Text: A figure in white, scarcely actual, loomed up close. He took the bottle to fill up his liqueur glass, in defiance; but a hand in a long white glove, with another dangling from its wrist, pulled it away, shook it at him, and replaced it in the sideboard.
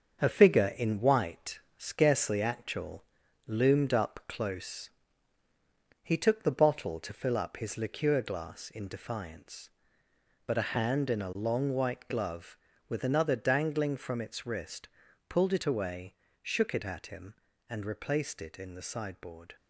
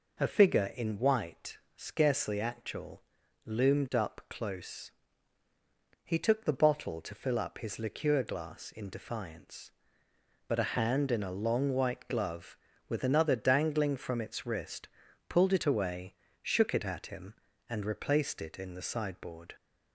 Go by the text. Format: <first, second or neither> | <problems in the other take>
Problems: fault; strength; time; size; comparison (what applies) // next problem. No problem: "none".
second | gets quieter; noticeable; throughout; 6 dB